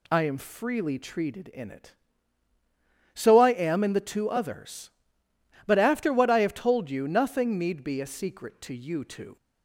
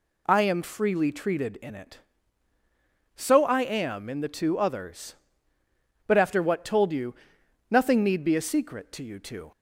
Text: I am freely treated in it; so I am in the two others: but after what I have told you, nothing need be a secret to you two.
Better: first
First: none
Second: skips "I have"; at 6.6 s

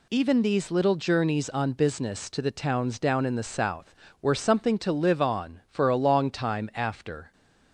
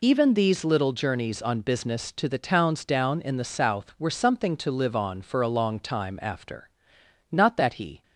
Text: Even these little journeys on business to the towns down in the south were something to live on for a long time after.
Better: first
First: none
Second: goes on to say "Not that he"; noticeable; from 7.3 s on; 0.70 s long

